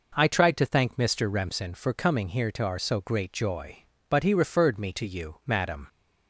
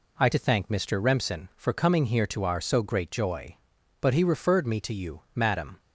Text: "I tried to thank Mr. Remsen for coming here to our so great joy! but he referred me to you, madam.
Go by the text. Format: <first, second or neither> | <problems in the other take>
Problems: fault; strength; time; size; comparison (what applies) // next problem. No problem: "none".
first | skips "tried"; at 0.3 s